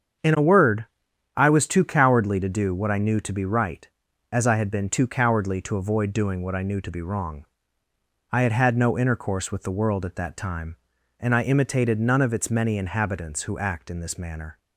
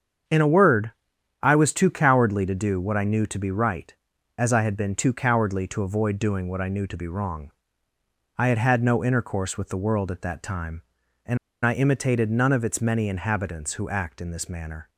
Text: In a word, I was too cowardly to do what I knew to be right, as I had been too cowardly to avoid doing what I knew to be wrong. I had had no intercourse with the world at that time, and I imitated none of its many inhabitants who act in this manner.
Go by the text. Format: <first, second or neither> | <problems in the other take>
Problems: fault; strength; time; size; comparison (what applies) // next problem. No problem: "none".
first | starts louder than the rest; strong; until 1.7 s; 7 dB; strong in the first // pauses between "and" and "I"; slight; at 11.3 s; 0.27 s long